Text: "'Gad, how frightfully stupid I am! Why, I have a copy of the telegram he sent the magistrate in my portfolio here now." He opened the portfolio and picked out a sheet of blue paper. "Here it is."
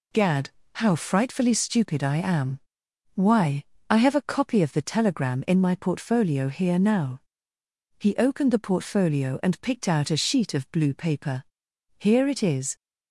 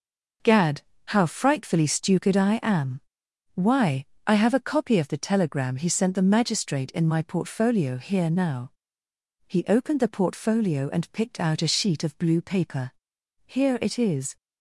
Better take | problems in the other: second | skips "he sent the magistrate"; at 5.4 s

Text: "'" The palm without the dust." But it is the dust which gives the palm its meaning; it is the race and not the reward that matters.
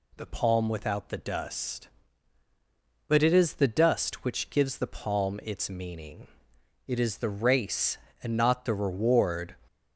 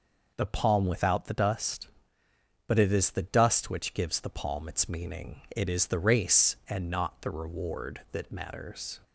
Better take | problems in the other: second | stops before "that matters"; at 9.6 s

